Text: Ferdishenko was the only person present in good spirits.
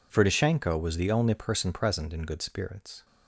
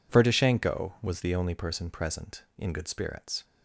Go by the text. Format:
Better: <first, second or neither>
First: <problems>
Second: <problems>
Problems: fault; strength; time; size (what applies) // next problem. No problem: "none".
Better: neither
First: none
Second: none